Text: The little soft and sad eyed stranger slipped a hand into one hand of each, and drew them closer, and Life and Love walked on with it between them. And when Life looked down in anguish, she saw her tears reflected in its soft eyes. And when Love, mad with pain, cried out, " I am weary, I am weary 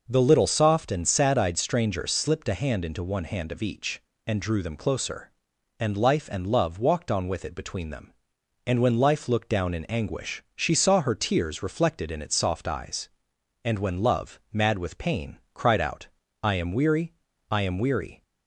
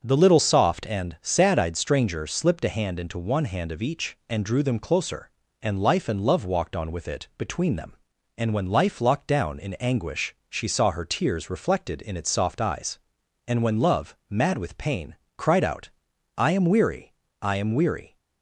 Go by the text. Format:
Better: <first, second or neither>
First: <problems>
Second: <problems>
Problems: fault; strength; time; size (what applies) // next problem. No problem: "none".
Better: first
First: none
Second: starts louder than the rest; until 1.0 s; 7 dB // says "locked" for "looked"; at 9.0 s